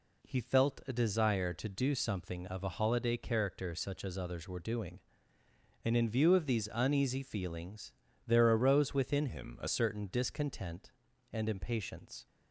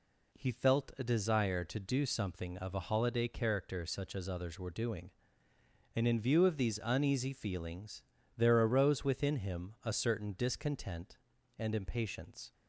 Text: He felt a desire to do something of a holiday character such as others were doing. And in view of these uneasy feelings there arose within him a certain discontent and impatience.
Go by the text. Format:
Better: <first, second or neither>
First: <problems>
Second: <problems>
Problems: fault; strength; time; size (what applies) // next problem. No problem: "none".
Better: second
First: pauses between "feelings" and "there"; slight; at 7.9 s; 0.36 s long // changes voice from "him" to "a"; from 9.2 to 9.6 s; 0.4 s long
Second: pauses between "feelings" and "there"; slight; at 8.0 s; 0.36 s long